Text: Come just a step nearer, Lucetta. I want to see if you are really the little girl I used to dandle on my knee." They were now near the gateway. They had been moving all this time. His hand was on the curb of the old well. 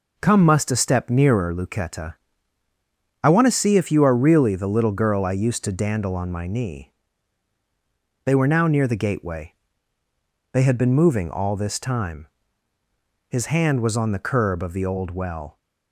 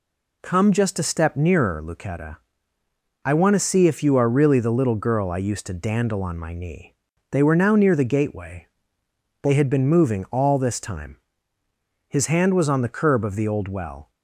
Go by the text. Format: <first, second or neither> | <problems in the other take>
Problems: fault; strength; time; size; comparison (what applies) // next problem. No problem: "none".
second | says "must" for "just"; at 0.4 s